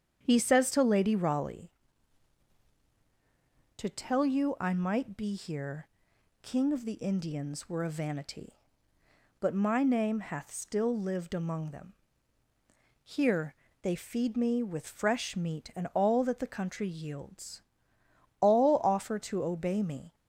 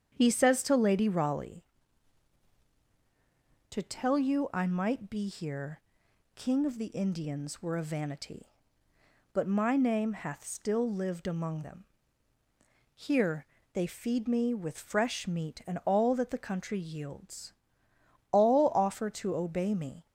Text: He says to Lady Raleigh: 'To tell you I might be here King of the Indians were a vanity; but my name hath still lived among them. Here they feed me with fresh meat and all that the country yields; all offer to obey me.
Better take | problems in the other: neither | starts louder than the rest; strong; the same in both // pauses between "here" and "King"; noticeable; the same in both // pauses between "Here" and "they"; slight; the same in both

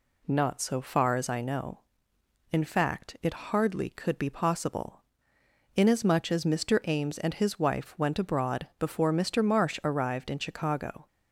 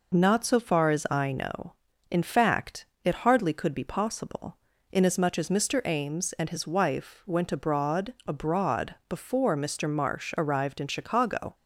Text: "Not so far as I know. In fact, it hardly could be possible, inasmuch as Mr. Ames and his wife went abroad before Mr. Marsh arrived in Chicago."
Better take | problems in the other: first | says "abroad" twice; at 8.2 s

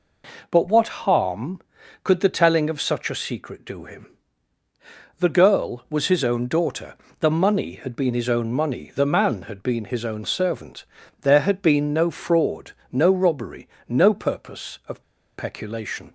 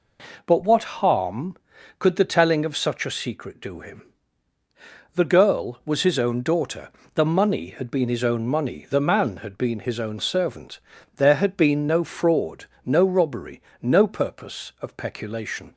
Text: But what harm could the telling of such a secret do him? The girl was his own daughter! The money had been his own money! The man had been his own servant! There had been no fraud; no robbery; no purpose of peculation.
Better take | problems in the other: second | pauses between "of" and "peculation"; slight; at 15.0 s; 0.33 s long

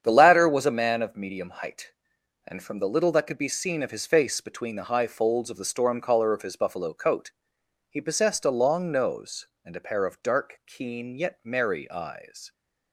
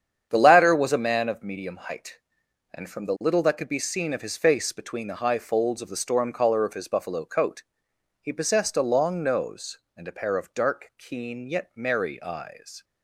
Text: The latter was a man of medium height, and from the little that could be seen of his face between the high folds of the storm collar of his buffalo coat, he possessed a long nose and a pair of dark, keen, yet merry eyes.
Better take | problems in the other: neither | starts louder than the rest; strong; the same in both

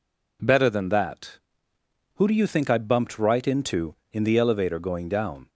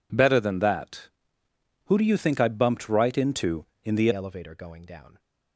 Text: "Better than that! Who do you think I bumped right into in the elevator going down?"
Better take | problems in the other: first | changes voice at "elevator"; from 4.1 s on; 1.0 s long

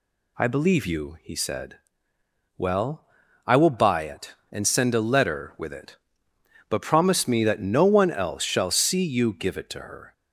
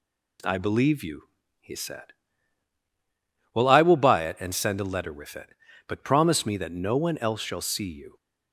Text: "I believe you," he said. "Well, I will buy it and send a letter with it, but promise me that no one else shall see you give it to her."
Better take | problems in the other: first | stops before "give it to her"; at 8.1 s

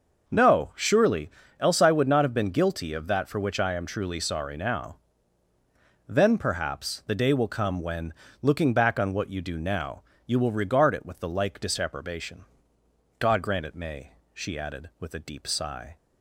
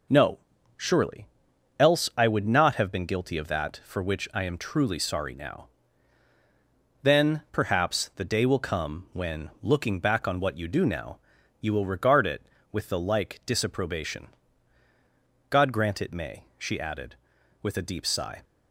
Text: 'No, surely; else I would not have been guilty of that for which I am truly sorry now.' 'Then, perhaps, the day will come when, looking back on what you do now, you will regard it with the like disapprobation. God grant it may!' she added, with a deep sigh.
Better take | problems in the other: neither | none

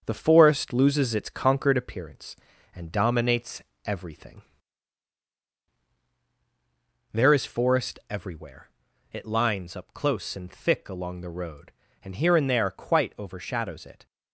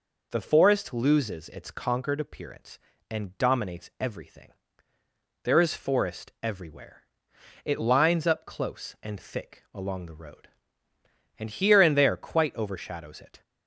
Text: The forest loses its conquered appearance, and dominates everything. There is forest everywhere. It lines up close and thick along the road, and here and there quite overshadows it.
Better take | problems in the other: second | gets quieter; noticeable; throughout; 5 dB // pauses between "dominates" and "everything"; slight; at 3.6 s; 0.22 s long

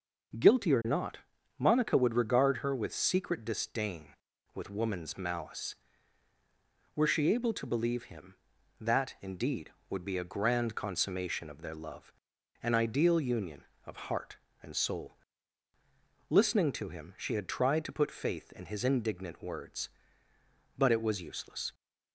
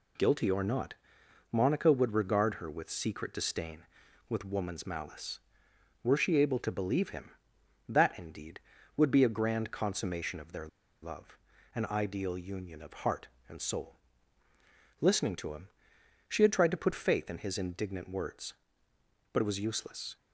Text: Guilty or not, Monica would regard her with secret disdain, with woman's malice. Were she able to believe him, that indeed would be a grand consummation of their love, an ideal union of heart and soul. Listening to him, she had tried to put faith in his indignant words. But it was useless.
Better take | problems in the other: first | pauses between "their" and "love"; slight; at 10.6 s; 0.35 s long

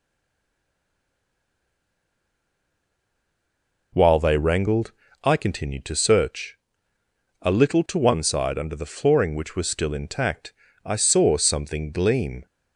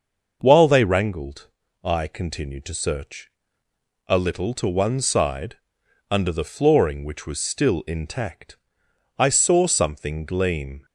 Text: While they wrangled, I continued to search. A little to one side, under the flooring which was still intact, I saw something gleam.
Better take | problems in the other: second | stays silent before the first word; strong; until 3.9 s; 3.9 s long

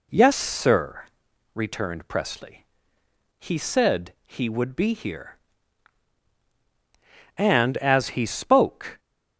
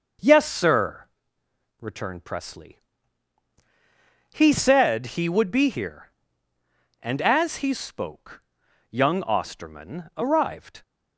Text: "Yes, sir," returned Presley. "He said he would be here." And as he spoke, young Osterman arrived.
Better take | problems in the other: second | stops before "young Osterman arrived"; at 8.9 s

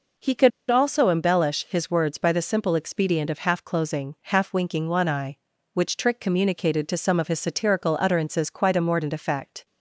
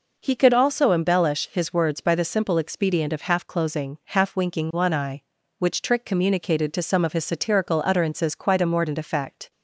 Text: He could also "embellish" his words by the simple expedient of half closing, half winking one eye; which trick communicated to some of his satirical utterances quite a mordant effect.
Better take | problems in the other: second | pauses between "could" and "also"; slight; at 0.5 s; 0.20 s long

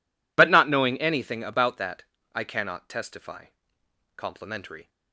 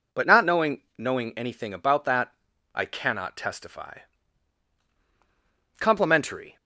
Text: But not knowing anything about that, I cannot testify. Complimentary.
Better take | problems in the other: first | says "knowing" twice; at 0.9 s

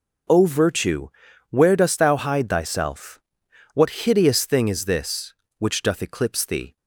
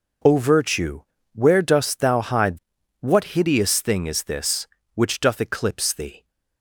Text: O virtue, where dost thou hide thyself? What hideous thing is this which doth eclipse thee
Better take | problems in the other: first | skips "thyself"; at 2.7 s

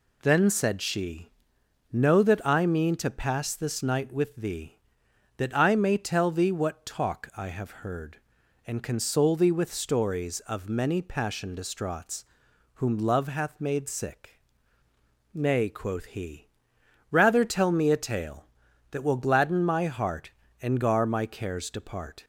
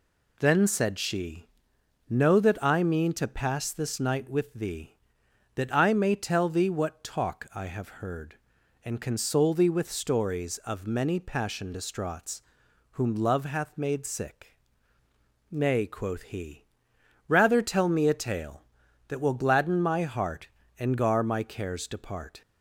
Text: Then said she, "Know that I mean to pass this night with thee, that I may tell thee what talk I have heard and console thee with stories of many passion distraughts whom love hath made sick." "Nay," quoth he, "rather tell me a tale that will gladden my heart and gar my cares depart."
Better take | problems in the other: neither | pauses between "distraughts" and "whom"; noticeable; the same in both

